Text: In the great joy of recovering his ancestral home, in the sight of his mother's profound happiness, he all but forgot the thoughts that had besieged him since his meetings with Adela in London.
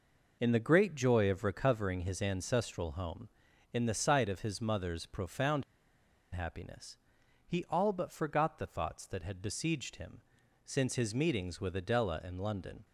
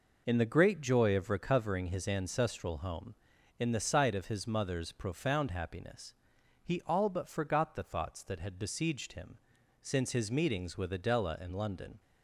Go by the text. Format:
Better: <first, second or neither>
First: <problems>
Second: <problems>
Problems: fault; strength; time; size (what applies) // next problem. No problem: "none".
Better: second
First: pauses between "profound" and "happiness"; noticeable; at 5.6 s; 0.69 s long // pauses between "him" and "since"; at 10.2 s; 0.44 s long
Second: pauses between "him" and "since"; at 9.3 s; 0.44 s long